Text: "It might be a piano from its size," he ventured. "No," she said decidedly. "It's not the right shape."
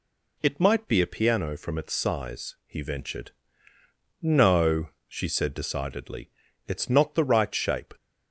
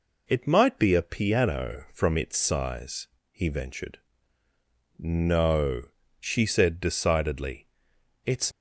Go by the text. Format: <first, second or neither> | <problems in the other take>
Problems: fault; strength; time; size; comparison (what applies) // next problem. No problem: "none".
first | stops before "not the right shape"; at 8.5 s